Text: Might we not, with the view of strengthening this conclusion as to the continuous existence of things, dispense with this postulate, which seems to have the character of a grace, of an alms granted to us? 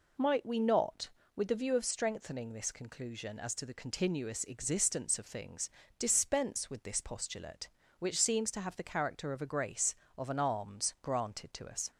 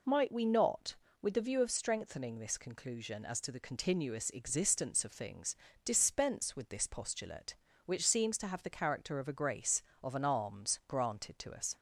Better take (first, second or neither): neither